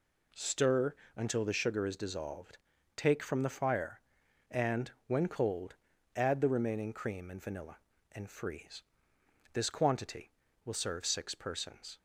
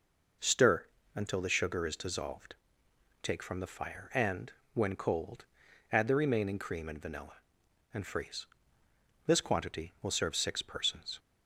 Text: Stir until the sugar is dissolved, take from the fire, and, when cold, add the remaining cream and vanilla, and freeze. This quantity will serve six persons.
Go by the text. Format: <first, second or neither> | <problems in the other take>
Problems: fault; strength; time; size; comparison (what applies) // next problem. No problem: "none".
neither | pauses between "Stir" and "until"; slight; the same in both